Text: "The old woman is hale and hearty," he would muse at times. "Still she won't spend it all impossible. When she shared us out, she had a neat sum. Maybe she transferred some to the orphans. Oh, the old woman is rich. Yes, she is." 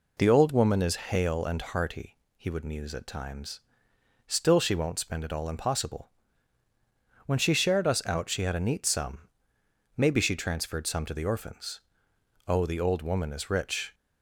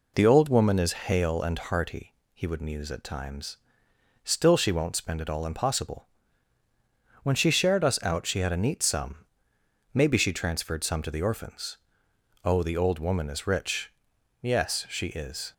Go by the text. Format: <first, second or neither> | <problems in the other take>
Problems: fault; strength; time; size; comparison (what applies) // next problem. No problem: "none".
second | stops before "Yes she is"; at 13.9 s